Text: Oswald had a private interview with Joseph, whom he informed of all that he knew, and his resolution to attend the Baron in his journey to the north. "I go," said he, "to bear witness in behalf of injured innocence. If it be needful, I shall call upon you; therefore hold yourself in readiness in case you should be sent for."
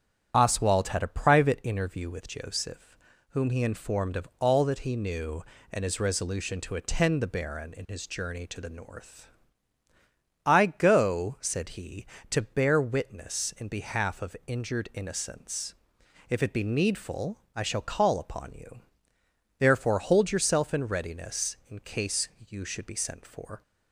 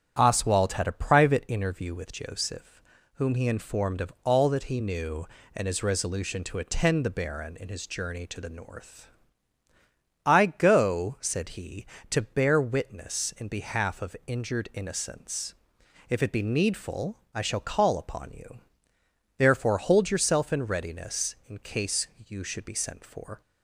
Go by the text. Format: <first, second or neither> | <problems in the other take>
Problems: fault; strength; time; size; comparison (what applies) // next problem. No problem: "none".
second | loses the start of "Oswald"; at 0.3 s; 30 ms // starts louder than the rest; strong; until 1.3 s; 9 dB; strong in the second // pauses between "case" and "you"; slight; at 22.2 s; 0.20 s long; slight in the second